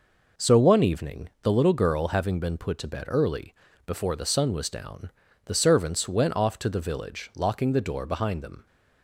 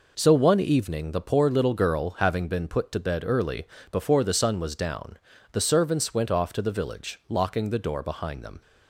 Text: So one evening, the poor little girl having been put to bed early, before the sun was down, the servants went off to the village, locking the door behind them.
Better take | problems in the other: second | skips "poor"; at 1.5 s

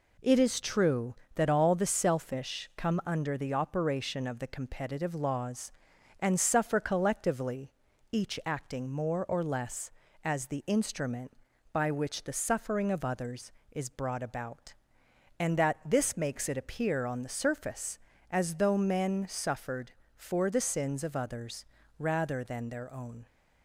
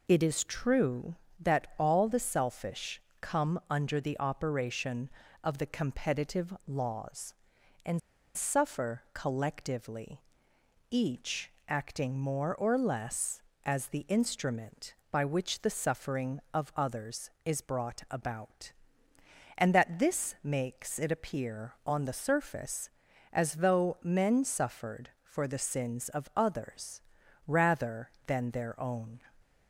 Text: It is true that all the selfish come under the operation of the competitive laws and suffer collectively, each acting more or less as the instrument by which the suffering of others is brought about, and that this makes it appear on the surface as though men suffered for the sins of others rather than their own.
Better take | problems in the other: first | pauses between "selfish" and "come"; slight; at 3.0 s; 0.20 s long // pauses between "and" and "suffer"; slight; at 7.9 s; 0.35 s long // pauses between "each" and "acting"; slight; at 11.4 s; 0.18 s long // pauses between "others" and "rather"; at 27.0 s; 0.44 s long; slight in the first

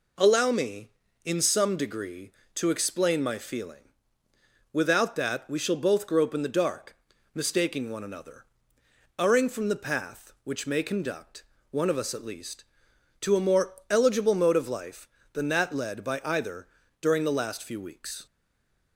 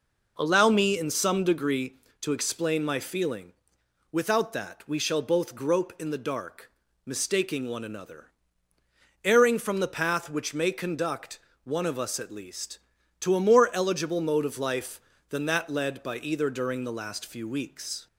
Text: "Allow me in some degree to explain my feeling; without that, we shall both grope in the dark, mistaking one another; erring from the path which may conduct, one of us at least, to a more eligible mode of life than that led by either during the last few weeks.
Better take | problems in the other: second | pauses between "more" and "eligible"; slight; at 13.7 s; 0.16 s long // pauses between "either" and "during"; slight; at 16.6 s; 0.32 s long // stays silent after the last word; slight; from 18.2 s on; 0.7 s long

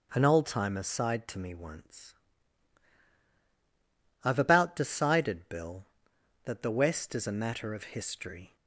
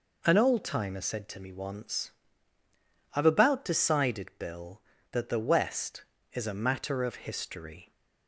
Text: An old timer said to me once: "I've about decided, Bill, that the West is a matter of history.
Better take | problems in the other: second | starts louder than the rest; until 1.1 s; 7 dB // says "sighed" for "said"; at 0.8 s

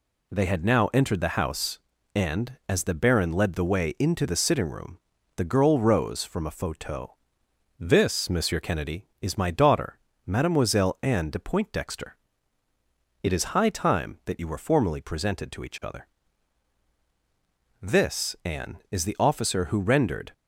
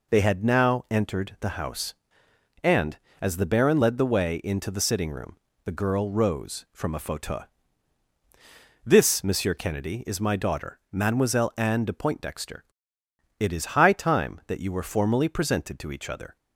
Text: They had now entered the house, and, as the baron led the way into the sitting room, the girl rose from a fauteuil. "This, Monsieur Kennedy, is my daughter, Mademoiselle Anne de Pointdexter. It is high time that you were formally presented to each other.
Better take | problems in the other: second | goes on to say "This Anne is the officer who rendered"; strong; from 17.8 s on; 2.5 s long

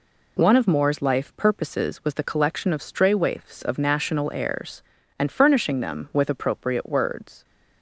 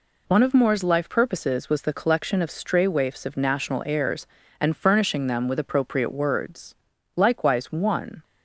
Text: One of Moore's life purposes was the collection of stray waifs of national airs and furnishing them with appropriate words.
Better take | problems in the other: first | goes on to say "Likewise one"; noticeable; from 7.1 s on; 1.0 s long

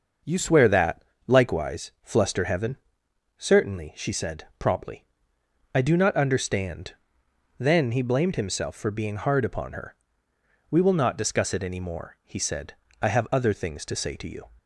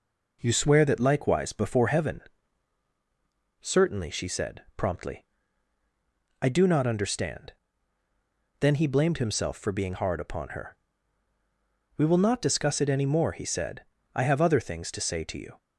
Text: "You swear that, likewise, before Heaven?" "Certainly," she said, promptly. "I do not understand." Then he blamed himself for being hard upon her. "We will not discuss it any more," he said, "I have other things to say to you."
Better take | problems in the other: second | starts louder than the rest; noticeable; until 1.5 s; 6 dB // says "fluster" for "before"; at 2.0 s

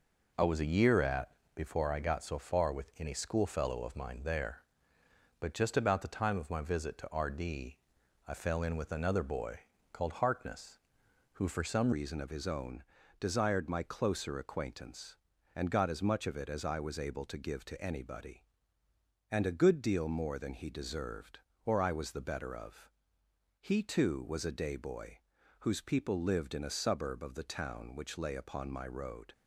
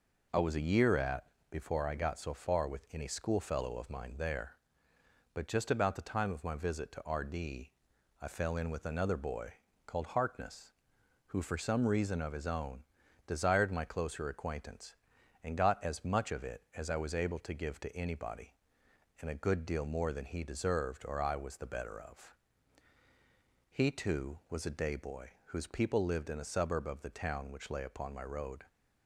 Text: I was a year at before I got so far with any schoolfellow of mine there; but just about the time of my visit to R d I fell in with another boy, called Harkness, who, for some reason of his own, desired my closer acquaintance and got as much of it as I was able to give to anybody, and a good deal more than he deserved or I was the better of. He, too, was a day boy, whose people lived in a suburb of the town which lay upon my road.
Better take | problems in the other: second | pauses between "at" and "before"; slight; at 1.2 s; 0.26 s long; slight in the second // pauses between "d" and "I"; noticeable; at 7.7 s; 0.48 s long; noticeable in the second // changes voice at "reason"; from 11.9 s on; 17.4 s long

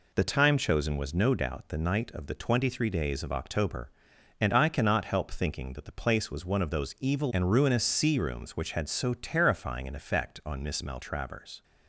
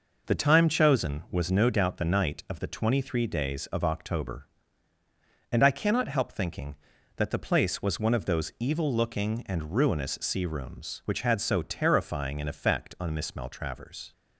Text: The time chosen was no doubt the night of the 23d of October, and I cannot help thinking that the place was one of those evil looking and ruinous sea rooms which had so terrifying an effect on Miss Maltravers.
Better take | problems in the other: second | skips "looking"; at 7.3 s

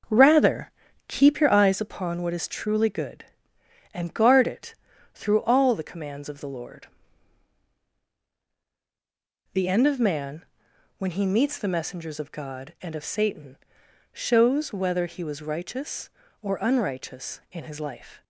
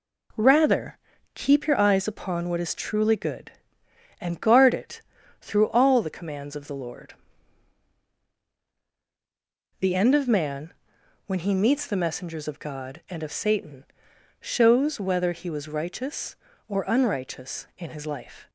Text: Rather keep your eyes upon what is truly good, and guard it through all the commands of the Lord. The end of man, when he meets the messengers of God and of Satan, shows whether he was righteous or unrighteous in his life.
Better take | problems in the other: second | starts louder than the rest; until 1.9 s; 6 dB // pauses between "Rather" and "keep"; slight; at 0.7 s; 0.36 s long; slight in the second // pauses between "it" and "through"; at 4.7 s; 0.40 s long; also in the second

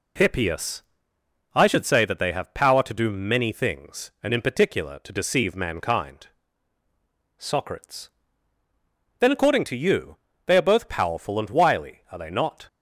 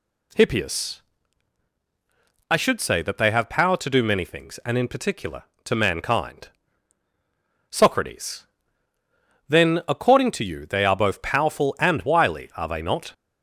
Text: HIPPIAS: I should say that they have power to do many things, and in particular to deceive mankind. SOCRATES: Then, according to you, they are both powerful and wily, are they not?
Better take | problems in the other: first | skips "deceive"; at 5.7 s

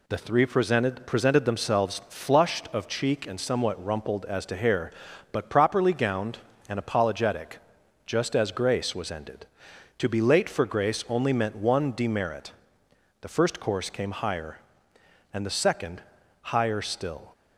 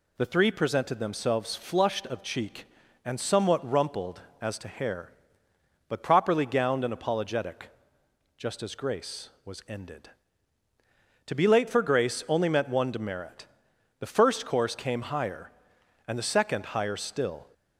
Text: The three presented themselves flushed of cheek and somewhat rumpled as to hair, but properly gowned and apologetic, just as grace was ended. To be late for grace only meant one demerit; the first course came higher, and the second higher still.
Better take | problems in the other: second | says "presented" twice; at 1.0 s // pauses between "second" and "higher"; at 16.0 s; 0.40 s long

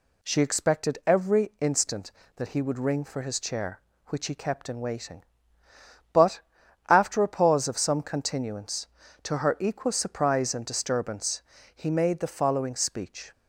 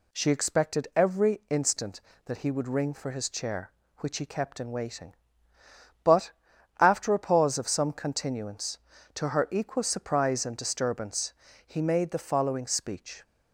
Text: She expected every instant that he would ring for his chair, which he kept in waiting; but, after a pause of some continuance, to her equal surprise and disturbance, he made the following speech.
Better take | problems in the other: neither | none

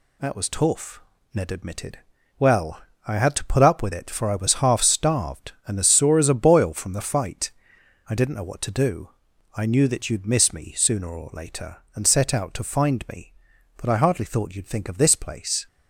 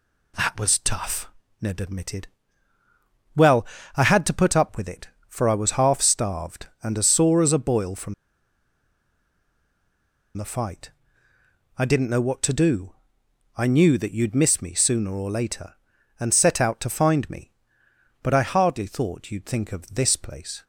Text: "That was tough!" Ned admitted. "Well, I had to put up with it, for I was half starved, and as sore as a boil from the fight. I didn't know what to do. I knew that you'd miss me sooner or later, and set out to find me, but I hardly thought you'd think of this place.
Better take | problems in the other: first | pauses between "from" and "the"; strong; at 8.1 s; 2.2 s long

